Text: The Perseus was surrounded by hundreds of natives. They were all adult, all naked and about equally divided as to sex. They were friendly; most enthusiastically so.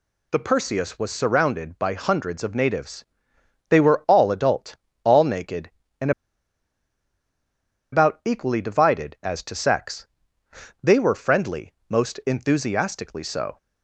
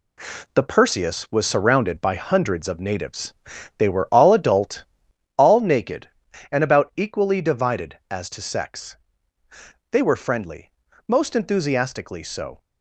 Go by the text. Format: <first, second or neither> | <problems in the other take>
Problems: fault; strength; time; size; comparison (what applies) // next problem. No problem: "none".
second | pauses between "and" and "about"; strong; at 6.1 s; 1.8 s long